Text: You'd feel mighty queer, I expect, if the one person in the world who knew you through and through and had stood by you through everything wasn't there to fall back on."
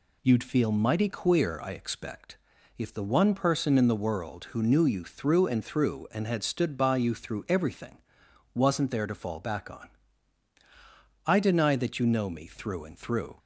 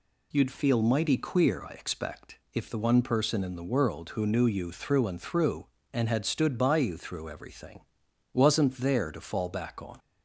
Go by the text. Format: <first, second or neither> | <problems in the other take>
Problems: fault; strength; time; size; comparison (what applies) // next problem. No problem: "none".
second | pauses between "everything" and "wasn't"; noticeable; at 7.9 s; 0.54 s long; noticeable in the second // goes on to say "I deny that you know me through and through"; strong; from 11.2 s on; 2.1 s long